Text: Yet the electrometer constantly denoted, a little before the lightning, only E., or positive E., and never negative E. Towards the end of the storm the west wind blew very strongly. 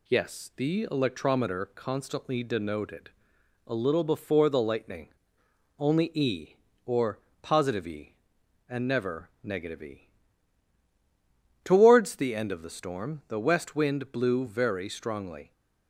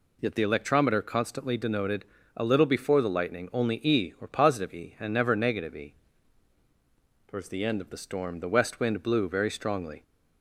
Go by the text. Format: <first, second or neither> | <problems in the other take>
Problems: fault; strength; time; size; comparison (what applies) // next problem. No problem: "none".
second | says "Yes" for "Yet"; at 0.0 s // pauses between "or" and "positive"; slight; at 7.1 s; 0.22 s long